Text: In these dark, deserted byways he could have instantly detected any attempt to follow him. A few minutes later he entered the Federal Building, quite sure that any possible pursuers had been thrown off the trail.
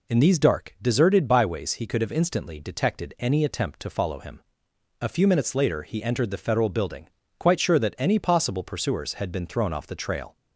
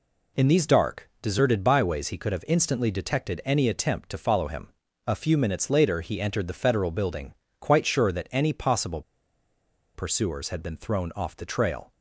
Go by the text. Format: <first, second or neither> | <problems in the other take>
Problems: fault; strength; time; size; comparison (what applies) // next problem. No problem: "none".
first | pauses between "possible" and "pursuers"; noticeable; at 9.0 s; 0.93 s long